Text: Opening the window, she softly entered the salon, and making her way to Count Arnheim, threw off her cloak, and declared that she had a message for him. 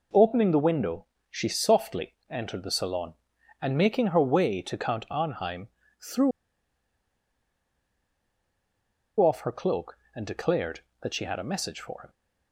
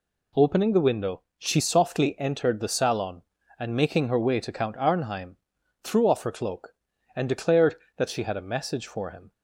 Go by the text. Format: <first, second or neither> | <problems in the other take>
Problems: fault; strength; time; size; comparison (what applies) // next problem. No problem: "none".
second | pauses between "threw" and "off"; strong; at 6.3 s; 2.8 s long